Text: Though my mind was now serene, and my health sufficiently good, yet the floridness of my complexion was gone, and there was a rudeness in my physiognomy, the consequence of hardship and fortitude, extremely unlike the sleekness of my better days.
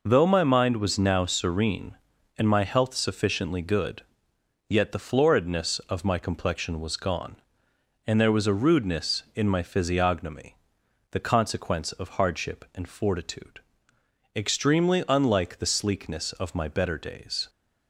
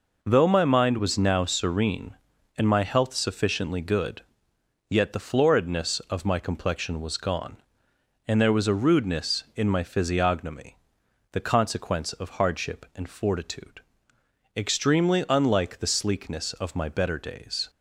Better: neither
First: none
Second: none

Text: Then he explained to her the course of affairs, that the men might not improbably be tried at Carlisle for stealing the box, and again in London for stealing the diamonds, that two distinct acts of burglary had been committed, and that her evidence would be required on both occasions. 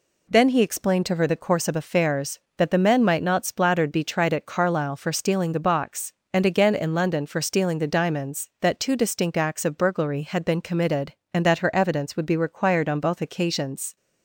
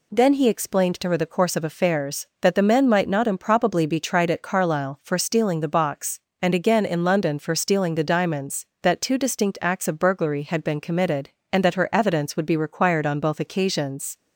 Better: second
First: says "splattered" for "improbably"; at 3.4 s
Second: none

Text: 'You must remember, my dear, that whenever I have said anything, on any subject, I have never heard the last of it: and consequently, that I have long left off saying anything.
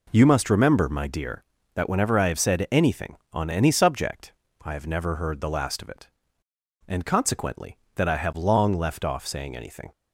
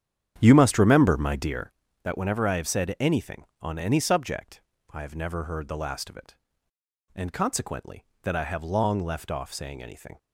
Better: first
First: none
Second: starts louder than the rest; strong; until 1.8 s; 9 dB

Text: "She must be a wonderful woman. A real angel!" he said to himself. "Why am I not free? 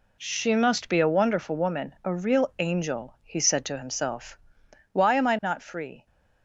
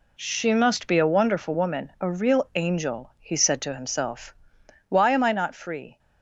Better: neither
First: none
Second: none

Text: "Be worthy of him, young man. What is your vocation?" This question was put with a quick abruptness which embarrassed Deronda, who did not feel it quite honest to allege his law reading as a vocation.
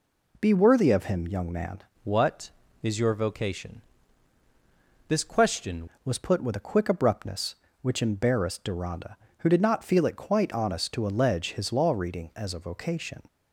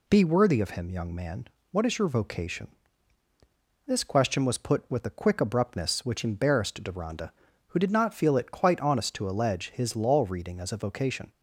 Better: second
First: changes voice from "What" to "question"; from 2.0 to 5.8 s; 3.8 s long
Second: none

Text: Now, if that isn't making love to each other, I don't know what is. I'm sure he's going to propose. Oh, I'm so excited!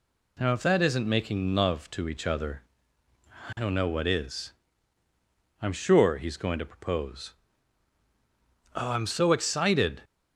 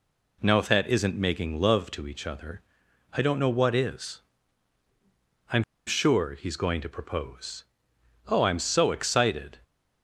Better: first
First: none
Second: pauses between "I'm" and "sure"; slight; at 5.6 s; 0.23 s long

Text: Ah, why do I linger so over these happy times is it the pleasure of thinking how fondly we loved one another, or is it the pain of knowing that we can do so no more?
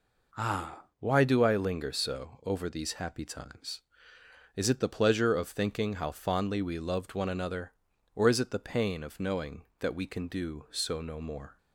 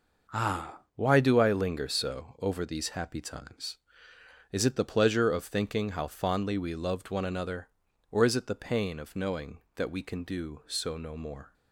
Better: first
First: none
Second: gets quieter; strong; throughout; 7.5 dB

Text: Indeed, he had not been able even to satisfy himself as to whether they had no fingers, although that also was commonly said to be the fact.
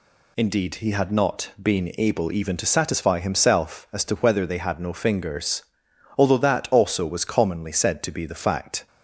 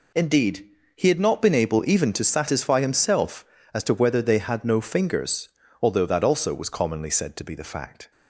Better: neither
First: none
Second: none

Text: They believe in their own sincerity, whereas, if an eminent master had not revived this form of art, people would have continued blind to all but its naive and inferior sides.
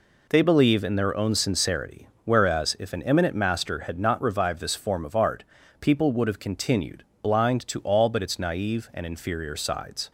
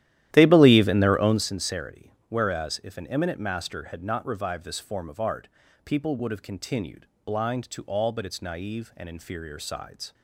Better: first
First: pauses between "continued" and "blind"; slight; at 7.0 s; 0.18 s long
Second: starts louder than the rest; strong; until 1.4 s; 13 dB // pauses between "continued" and "blind"; slight; at 7.0 s; 0.18 s long

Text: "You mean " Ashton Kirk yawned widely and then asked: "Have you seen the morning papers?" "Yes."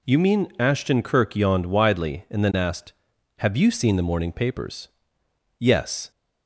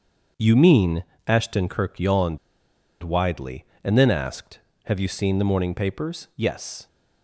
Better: first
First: none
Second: starts louder than the rest; until 1.4 s; 7 dB // pauses between "yawned" and "widely"; noticeable; at 2.3 s; 0.64 s long

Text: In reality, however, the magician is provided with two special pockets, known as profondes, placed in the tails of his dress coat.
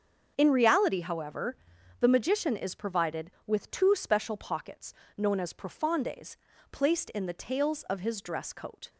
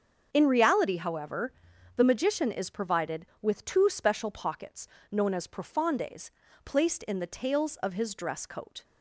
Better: neither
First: starts louder than the rest; until 1.3 s; 7 dB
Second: starts louder than the rest; until 1.3 s; 7 dB

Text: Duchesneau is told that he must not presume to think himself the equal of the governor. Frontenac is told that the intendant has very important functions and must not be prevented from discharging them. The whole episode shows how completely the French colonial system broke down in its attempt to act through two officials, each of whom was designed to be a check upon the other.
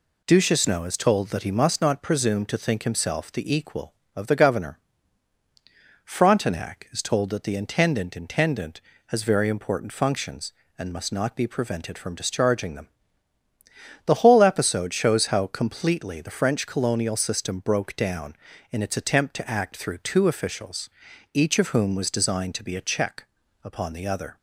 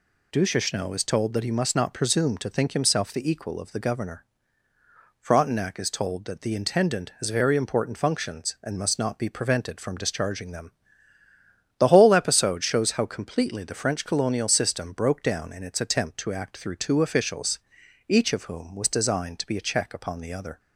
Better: second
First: says "intendant" twice; at 8.1 s // pauses between "check" and "upon"; at 23.2 s; 0.40 s long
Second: none

